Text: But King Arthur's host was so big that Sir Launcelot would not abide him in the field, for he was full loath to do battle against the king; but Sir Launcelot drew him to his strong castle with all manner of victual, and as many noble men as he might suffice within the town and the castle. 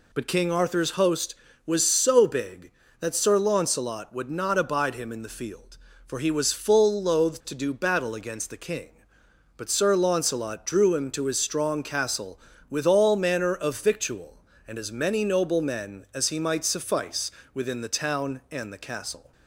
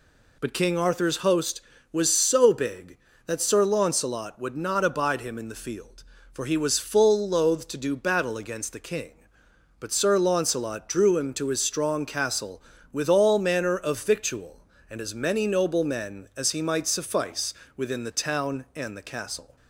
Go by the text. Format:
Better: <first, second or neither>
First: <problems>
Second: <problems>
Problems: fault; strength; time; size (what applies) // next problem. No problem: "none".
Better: neither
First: pauses between "suffice" and "within"; slight; at 17.3 s; 0.24 s long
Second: pauses between "suffice" and "within"; slight; at 17.5 s; 0.24 s long